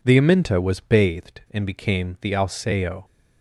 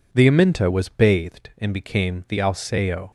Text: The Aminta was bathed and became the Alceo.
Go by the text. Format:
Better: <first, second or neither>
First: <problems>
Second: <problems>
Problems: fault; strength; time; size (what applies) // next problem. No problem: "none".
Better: neither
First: none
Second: none